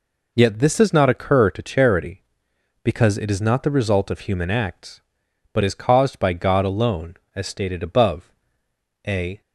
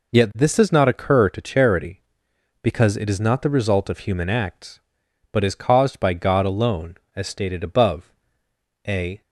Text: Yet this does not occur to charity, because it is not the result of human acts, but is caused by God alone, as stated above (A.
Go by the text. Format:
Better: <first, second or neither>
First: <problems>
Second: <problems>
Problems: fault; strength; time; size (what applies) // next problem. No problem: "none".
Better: neither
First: none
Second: none